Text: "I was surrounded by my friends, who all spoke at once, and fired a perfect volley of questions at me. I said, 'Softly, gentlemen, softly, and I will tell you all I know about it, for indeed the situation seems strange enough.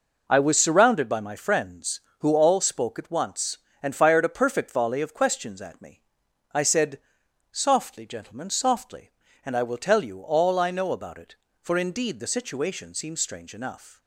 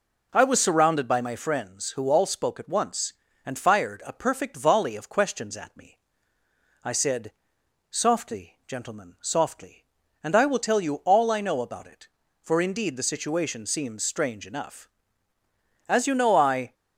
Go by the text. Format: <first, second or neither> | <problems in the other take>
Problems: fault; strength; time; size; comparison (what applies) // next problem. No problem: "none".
first | goes on to say "As you know I"; noticeable; from 15.8 s on; 0.86 s long